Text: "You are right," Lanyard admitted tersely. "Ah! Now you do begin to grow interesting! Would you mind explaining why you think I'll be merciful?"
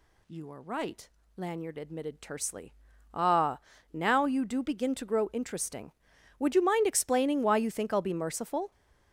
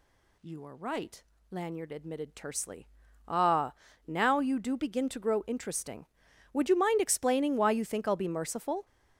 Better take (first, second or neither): neither